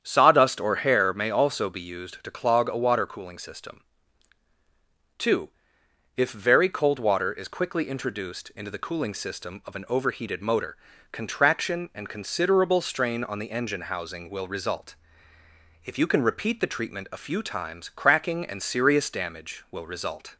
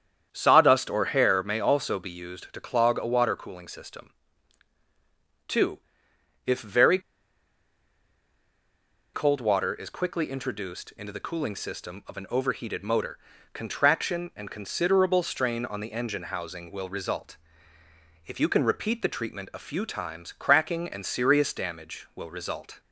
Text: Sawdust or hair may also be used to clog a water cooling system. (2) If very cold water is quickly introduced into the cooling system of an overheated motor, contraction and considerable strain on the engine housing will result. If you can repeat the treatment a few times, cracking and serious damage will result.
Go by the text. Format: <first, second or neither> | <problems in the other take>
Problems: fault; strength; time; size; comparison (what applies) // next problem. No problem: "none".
first | starts louder than the rest; strong; until 1.3 s; 8.5 dB; strong in the first // pauses between "very" and "cold"; strong; at 6.9 s; 2.1 s long